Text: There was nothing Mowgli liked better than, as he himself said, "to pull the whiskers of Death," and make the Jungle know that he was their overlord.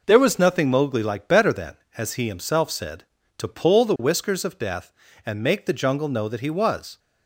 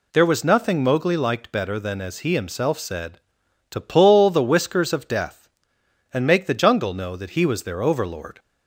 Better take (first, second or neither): second